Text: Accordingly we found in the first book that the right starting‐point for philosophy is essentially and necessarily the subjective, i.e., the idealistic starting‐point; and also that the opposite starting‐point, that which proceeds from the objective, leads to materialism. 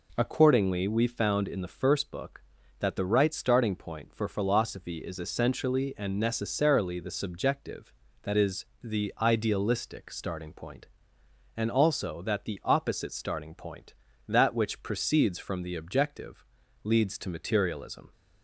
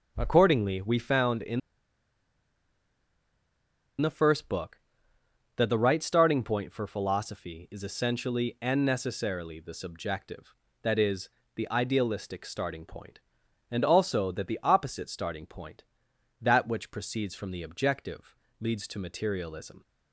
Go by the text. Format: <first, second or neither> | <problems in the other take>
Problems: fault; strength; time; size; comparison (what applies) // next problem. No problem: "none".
first | starts louder than the rest; until 1.1 s; 6.5 dB // pauses between "in" and "the"; strong; at 1.5 s; 2.4 s long